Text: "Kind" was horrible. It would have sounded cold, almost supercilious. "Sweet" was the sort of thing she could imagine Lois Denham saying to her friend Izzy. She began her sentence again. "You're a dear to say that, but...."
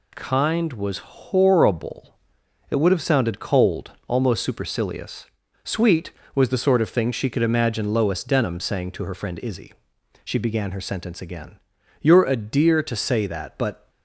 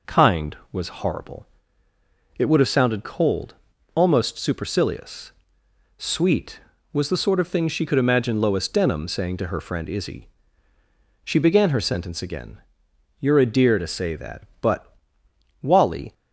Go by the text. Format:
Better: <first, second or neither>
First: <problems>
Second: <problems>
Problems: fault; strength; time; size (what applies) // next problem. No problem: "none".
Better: first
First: none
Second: goes on to say "Wally"; from 15.6 s on; 0.50 s long